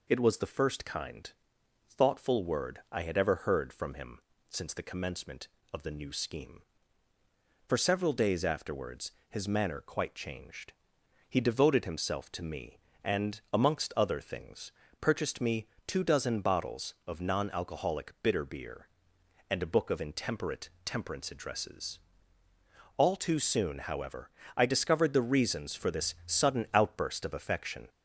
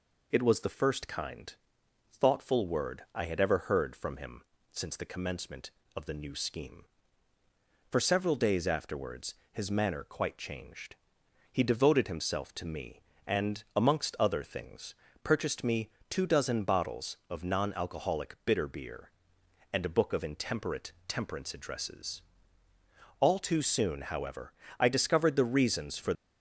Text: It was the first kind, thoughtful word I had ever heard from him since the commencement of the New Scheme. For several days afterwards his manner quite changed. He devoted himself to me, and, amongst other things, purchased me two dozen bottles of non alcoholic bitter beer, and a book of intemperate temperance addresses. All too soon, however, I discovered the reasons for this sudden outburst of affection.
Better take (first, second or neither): first